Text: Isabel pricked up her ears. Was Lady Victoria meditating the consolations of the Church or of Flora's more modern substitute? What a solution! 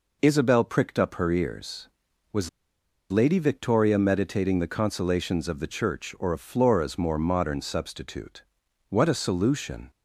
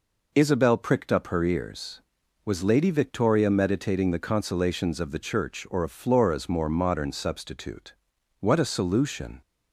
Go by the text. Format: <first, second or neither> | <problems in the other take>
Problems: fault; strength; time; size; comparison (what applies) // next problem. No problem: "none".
second | pauses between "Was" and "Lady"; noticeable; at 2.4 s; 0.62 s long